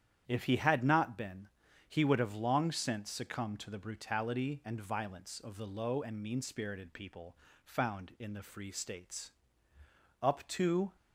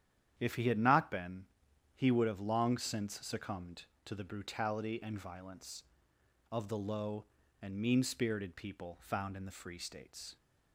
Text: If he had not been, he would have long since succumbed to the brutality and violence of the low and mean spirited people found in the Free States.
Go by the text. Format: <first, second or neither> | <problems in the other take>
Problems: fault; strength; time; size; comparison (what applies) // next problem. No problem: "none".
second | starts louder than the rest; strong; until 1.2 s; 9.5 dB; strong in the second // pauses between "people" and "found"; slight; at 7.3 s; 0.28 s long // goes on to say "Up to"; noticeable; from 10.2 s on; 0.74 s long